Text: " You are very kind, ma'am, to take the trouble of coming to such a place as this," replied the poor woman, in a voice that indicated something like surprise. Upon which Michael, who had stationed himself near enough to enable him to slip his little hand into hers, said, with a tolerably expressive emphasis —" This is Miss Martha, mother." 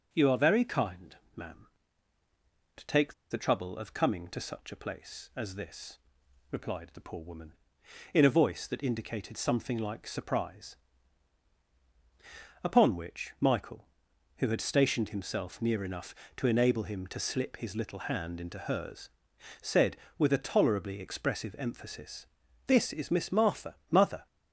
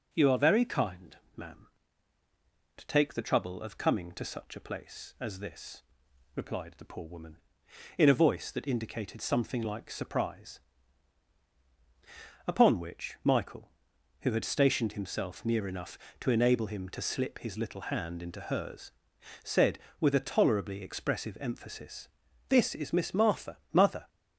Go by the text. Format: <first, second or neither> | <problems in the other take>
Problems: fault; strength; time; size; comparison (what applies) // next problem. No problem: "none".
second | starts louder than the rest; until 1.1 s; 6 dB; also in the second // pauses between "take" and "the"; slight; at 3.1 s; 0.16 s long